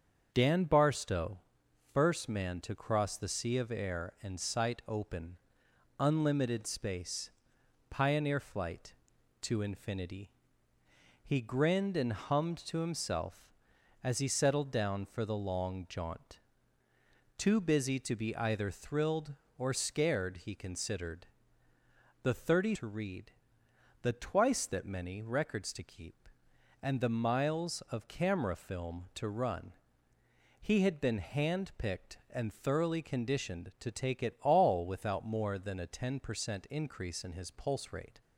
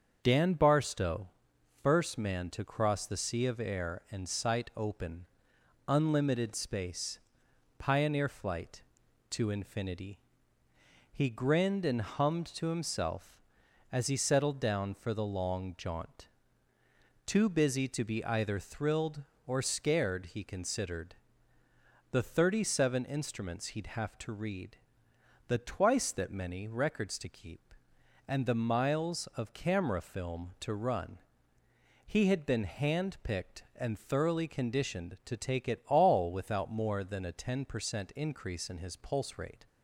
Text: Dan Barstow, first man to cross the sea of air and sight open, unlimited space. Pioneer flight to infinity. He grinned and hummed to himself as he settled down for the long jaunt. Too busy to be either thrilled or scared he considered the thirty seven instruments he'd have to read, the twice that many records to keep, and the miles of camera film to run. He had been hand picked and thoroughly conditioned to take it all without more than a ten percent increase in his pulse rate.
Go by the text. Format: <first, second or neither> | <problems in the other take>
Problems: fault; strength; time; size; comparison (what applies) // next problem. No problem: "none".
second | starts louder than the rest; strong; until 1.3 s; 7 dB; also in the second // pauses between "considered" and "the"; noticeable; at 21.2 s; 0.98 s long; noticeable in the second // skips "seven instruments he'd have"; at 22.7 s